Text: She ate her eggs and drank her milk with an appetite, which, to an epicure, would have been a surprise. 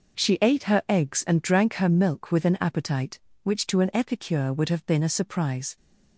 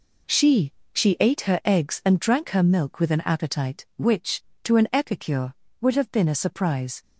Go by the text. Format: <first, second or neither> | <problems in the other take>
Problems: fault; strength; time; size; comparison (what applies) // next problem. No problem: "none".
first | says "She" twice; at 0.9 s